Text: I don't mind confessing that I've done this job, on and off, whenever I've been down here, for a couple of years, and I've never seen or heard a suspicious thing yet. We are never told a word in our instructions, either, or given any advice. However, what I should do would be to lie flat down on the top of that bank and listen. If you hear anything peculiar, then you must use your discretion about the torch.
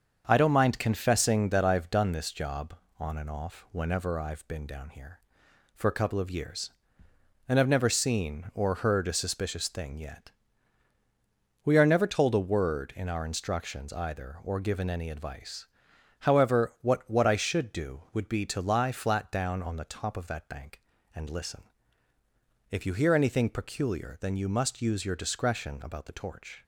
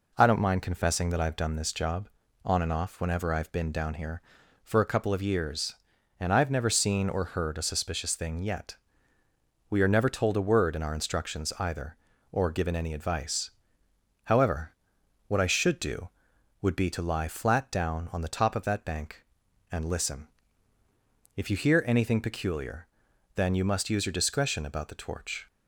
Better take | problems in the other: second | starts louder than the rest; until 1.2 s; 7 dB // says "what" twice; at 17.0 s

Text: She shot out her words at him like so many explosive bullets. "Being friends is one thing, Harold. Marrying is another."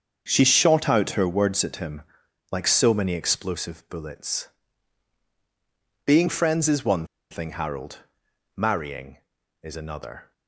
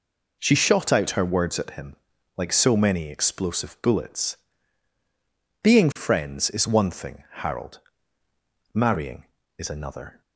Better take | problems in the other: second | starts louder than the rest; until 1.2 s; 7 dB // pauses between "him" and "like"; noticeable; at 2.0 s; 0.50 s long; also in the second // pauses between "one" and "thing"; slight; at 7.0 s; 0.24 s long

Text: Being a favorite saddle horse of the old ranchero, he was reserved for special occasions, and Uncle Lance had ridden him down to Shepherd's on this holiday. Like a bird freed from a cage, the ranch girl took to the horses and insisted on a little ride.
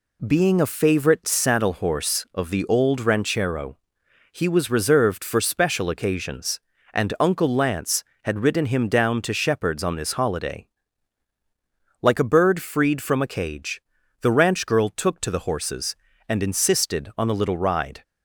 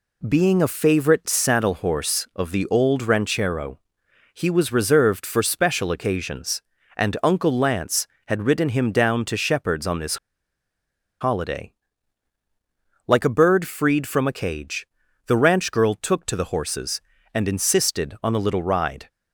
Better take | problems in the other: first | pauses between "this" and "holiday"; at 10.1 s; 1.0 s long

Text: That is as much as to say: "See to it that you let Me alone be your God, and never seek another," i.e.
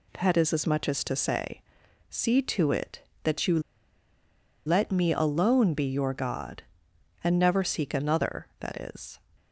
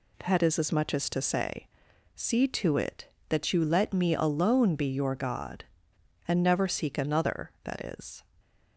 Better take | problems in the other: second | pauses between "you" and "let"; at 3.5 s; 1.0 s long

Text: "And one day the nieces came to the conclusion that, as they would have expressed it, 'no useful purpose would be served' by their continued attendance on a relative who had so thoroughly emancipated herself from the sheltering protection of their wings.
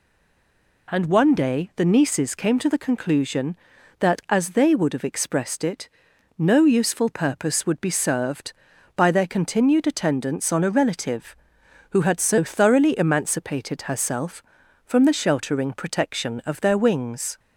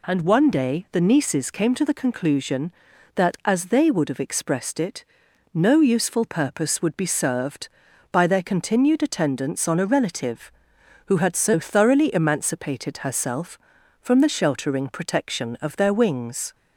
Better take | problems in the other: second | stays silent before the first word; slight; until 0.8 s; 0.8 s long

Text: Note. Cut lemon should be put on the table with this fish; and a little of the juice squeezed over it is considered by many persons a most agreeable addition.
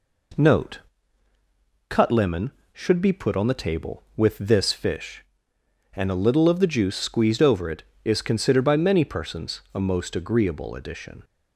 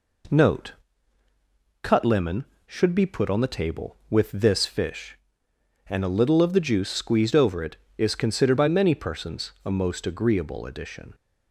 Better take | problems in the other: neither | none

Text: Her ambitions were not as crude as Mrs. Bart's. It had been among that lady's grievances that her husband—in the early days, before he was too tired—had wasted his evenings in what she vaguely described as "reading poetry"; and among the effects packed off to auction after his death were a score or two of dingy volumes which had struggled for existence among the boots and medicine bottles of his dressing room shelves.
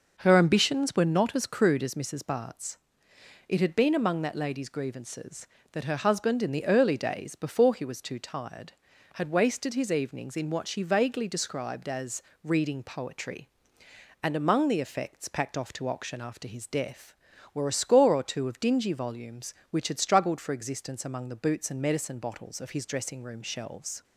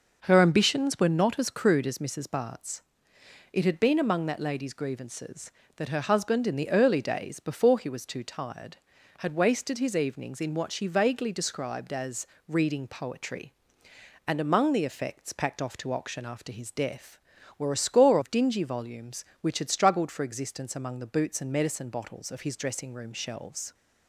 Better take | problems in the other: first | pauses between "as" and "reading"; slight; at 12.2 s; 0.22 s long; slight in the first // skips "or two"; at 18.1 s

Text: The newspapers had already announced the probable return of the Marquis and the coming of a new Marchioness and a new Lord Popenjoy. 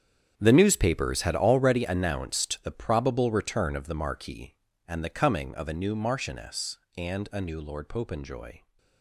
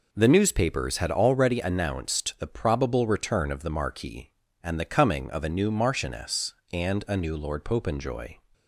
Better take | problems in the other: second | gets quieter; strong; throughout; 14 dB

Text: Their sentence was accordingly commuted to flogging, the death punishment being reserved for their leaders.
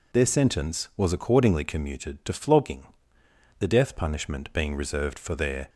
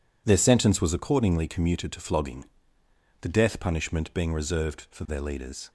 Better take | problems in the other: second | stops before "leaders"; at 5.6 s

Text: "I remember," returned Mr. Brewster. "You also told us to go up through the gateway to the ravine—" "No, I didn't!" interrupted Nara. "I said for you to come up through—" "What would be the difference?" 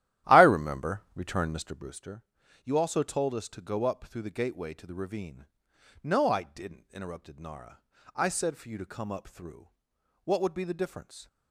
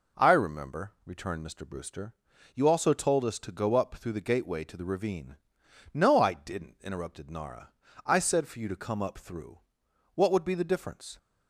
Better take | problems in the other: second | starts louder than the rest; strong; until 2.0 s; 13 dB

